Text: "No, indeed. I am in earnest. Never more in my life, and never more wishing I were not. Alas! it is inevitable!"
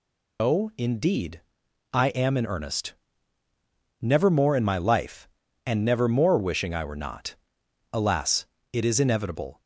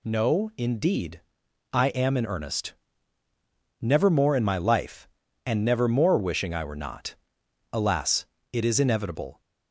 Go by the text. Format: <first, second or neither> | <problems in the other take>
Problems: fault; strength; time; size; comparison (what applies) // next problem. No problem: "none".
second | loses the start of "No"; at 0.3 s; 160 ms